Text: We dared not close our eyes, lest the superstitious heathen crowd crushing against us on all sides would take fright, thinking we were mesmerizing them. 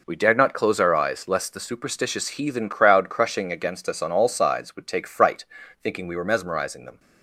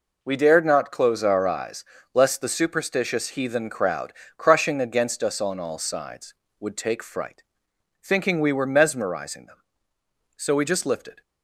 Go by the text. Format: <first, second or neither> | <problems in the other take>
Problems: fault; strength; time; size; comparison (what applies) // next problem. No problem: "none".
first | pauses between "crowd" and "crushing"; slight; at 4.1 s; 0.24 s long // goes on to say "So we just lifted"; noticeable; from 10.3 s on; 0.84 s long